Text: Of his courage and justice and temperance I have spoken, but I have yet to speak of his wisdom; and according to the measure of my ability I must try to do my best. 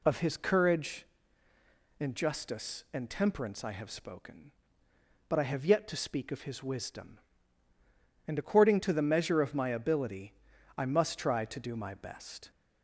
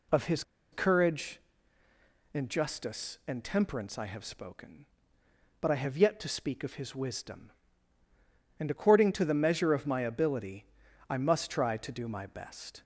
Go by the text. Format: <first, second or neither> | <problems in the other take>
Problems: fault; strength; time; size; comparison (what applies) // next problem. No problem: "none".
first | pauses between "his" and "courage"; slight; at 0.4 s; 0.29 s long // pauses between "ability" and "I"; at 10.6 s; 0.42 s long; also in the first